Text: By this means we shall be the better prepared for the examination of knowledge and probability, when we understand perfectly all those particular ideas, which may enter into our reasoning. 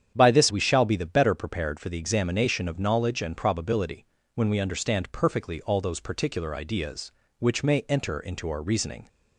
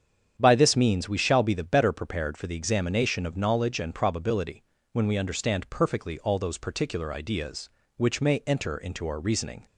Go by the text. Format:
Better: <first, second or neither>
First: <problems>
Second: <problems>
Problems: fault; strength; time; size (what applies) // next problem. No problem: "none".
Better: second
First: starts louder than the rest; strong; until 1.1 s; 8.5 dB // skips "means"; at 0.5 s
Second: starts louder than the rest; strong; until 1.4 s; 8.5 dB